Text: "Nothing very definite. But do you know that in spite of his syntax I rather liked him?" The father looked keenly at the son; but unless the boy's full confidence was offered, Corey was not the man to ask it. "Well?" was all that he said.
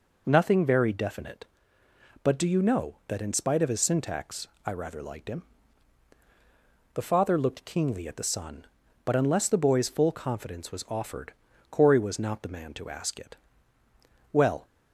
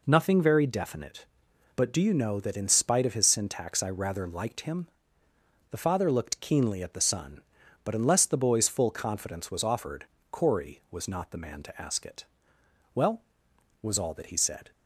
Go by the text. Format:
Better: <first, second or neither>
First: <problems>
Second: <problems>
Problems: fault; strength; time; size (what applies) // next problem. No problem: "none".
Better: second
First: pauses between "syntax" and "I"; slight; at 4.4 s; 0.18 s long // stops before "was all that he said"; at 14.6 s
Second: none